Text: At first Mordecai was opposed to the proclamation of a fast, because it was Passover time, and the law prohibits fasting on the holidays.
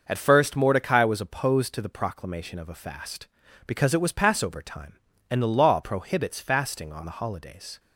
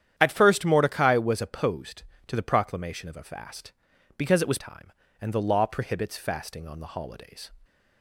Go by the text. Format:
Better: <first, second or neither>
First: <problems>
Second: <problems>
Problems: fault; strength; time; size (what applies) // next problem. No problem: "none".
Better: first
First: starts louder than the rest; noticeable; until 1.0 s; 6 dB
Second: starts louder than the rest; strong; until 1.1 s; 10 dB // skips "Passover"; at 4.5 s